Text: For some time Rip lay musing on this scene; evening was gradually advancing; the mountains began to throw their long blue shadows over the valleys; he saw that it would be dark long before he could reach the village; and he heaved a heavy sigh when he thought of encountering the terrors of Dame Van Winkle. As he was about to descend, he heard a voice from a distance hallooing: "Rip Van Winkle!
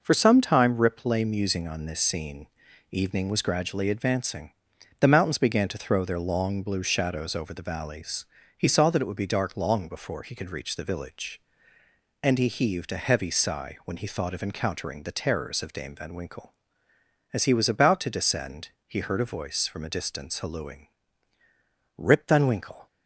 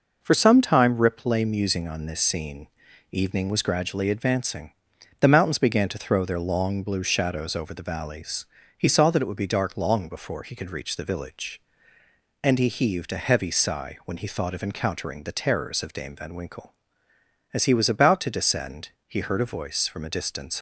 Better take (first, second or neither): first